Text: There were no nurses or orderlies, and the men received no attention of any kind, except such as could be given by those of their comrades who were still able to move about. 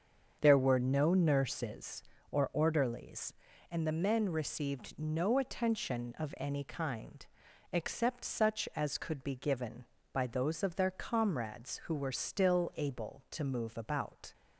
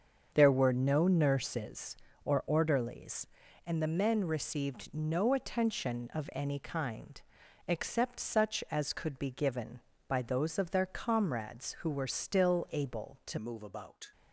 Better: first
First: starts louder than the rest; until 1.4 s; 7 dB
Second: starts louder than the rest; until 1.3 s; 7 dB // changes voice at "move"; from 13.3 s on; 0.8 s long

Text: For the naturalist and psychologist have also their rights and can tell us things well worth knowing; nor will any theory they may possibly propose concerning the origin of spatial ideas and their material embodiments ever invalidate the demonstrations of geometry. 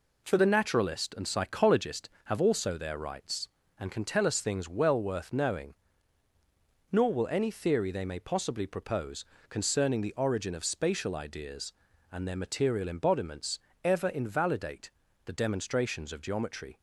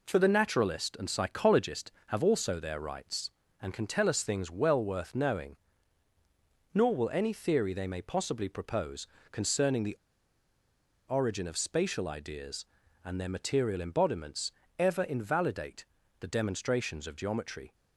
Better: first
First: pauses between "propose" and "concerning"; slight; at 9.2 s; 0.26 s long // pauses between "embodiments" and "ever"; slight; at 13.5 s; 0.26 s long // pauses between "invalidate" and "the"; slight; at 14.8 s; 0.36 s long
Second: pauses between "propose" and "concerning"; slight; at 9.0 s; 0.26 s long // pauses between "the" and "origin"; at 9.9 s; 1.1 s long // pauses between "embodiments" and "ever"; slight; at 14.5 s; 0.28 s long // pauses between "invalidate" and "the"; slight; at 15.8 s; 0.36 s long

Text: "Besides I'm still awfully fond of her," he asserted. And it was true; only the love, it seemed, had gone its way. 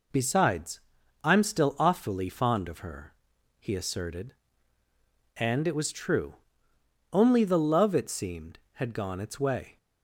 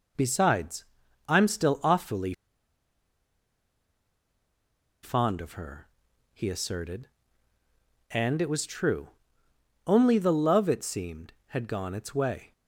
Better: first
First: pauses between "Besides" and "I'm"; at 0.8 s; 0.42 s long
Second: pauses between "Besides" and "I'm"; at 0.8 s; 0.42 s long // pauses between "awfully" and "fond"; strong; at 2.3 s; 2.7 s long

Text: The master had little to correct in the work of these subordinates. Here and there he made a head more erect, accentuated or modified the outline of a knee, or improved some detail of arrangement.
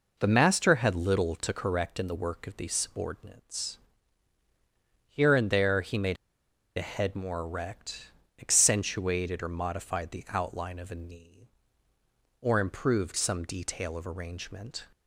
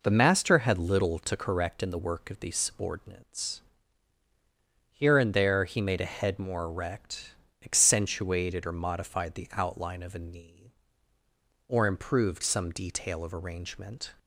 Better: second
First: pauses between "made" and "a"; noticeable; at 6.1 s; 0.60 s long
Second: none

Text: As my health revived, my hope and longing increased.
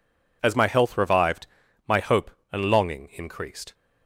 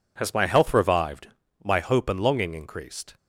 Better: first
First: none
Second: says "Has" for "As"; at 0.1 s

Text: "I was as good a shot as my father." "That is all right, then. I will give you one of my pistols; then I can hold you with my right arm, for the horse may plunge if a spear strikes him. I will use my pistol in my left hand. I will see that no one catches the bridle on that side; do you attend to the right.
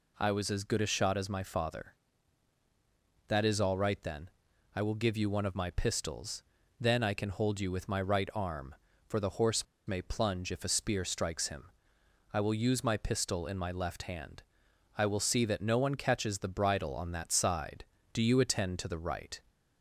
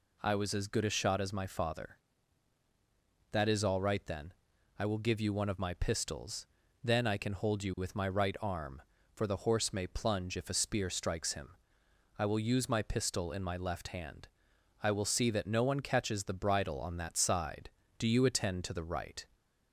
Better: second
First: pauses between "horse" and "may"; slight; at 9.6 s; 0.22 s long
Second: none

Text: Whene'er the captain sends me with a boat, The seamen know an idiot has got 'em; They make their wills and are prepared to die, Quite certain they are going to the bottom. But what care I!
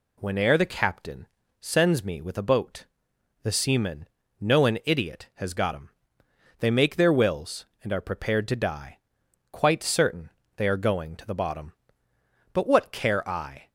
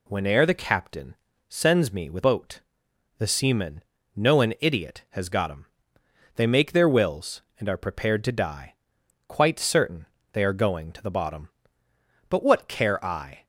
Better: first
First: pauses between "captain" and "sends"; slight; at 1.2 s; 0.32 s long // pauses between "seamen" and "know"; slight; at 4.0 s; 0.32 s long // pauses between "certain" and "they"; slight; at 10.3 s; 0.26 s long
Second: pauses between "captain" and "sends"; slight; at 1.1 s; 0.32 s long // skips "a"; at 2.2 s // pauses between "seamen" and "know"; slight; at 3.8 s; 0.32 s long // pauses between "certain" and "they"; slight; at 10.0 s; 0.26 s long

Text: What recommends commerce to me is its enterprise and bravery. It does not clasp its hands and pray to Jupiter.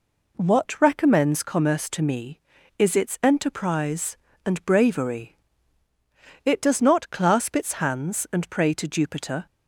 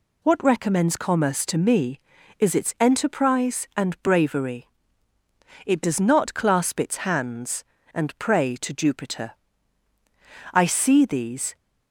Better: first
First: none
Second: goes on to say "I see these"; noticeable; from 10.5 s on; 1.0 s long

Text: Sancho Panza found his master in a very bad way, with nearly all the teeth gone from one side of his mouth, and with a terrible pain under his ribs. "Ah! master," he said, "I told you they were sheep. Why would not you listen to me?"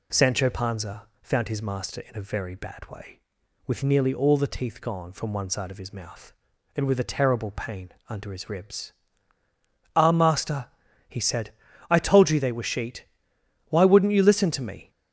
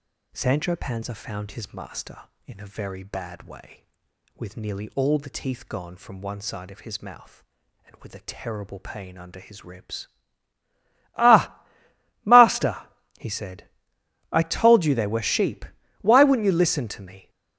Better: second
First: pauses between "Panza" and "found"; slight; at 1.0 s; 0.16 s long // pauses between "pain" and "under"; slight; at 7.9 s; 0.16 s long // says "sheet" for "sheep"; at 12.6 s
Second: none

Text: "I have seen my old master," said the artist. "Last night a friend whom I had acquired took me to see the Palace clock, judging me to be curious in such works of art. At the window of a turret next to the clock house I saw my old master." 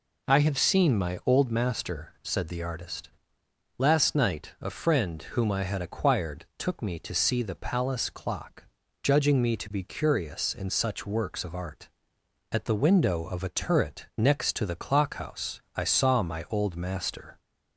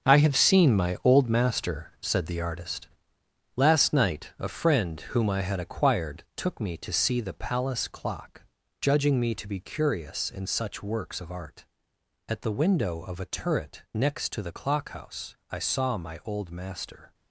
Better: first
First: none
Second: gets quieter; strong; throughout; 10.5 dB

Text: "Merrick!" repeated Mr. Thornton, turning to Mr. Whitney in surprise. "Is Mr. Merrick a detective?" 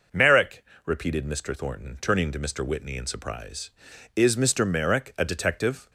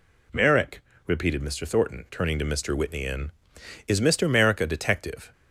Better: first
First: none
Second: skips "surprise"; at 3.5 s

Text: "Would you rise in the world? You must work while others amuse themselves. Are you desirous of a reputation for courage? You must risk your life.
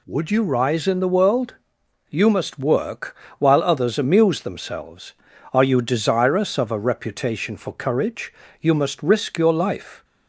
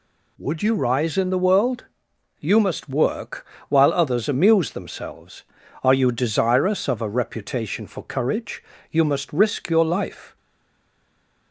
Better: first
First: pauses between "work" and "while"; slight; at 3.1 s; 0.22 s long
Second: pauses between "work" and "while"; slight; at 3.4 s; 0.22 s long // stays silent after the last word; noticeable; from 10.3 s on; 1.2 s long

